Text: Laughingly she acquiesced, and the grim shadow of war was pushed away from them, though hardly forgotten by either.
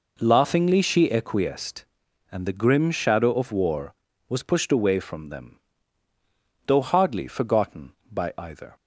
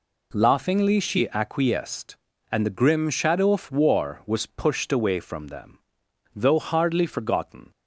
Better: first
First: none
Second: stops before "by either"; at 7.7 s

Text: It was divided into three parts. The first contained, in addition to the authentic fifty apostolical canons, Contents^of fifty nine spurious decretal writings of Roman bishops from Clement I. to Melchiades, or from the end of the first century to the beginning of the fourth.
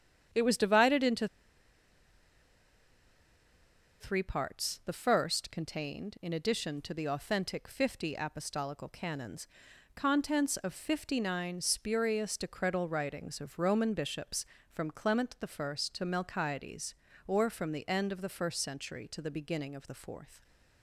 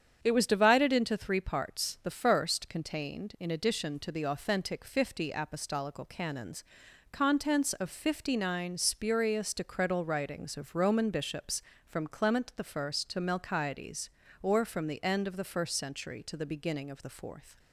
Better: second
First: starts louder than the rest; strong; until 4.0 s; 8.5 dB // pauses between "into" and "three"; strong; at 1.2 s; 2.7 s long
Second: starts louder than the rest; strong; until 1.2 s; 8 dB

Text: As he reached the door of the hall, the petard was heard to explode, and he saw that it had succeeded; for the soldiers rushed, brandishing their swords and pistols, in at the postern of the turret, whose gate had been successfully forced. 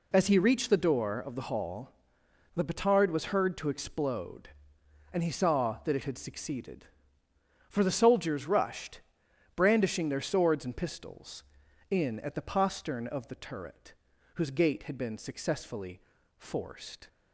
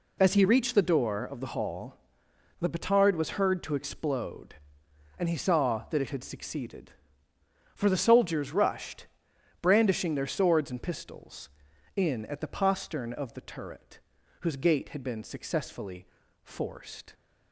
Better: neither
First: pauses between "successfully" and "forced"; slight; at 16.0 s; 0.34 s long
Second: pauses between "successfully" and "forced"; slight; at 16.0 s; 0.34 s long

